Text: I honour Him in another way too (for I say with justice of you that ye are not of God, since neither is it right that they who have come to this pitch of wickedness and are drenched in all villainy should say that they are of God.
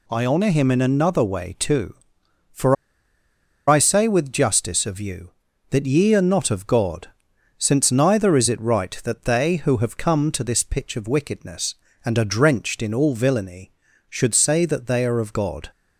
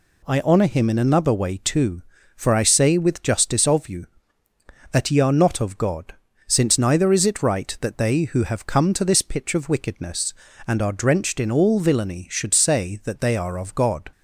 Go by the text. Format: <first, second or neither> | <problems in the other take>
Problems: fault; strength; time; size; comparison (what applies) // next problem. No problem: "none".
second | pauses between "for" and "I"; noticeable; at 2.7 s; 0.93 s long